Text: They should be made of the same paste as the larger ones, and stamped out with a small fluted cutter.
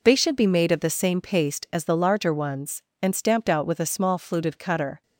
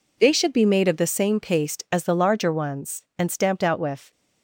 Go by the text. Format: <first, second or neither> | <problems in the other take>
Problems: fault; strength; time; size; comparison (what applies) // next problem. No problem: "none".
first | stops before "a small fluted cutter"; at 4.1 s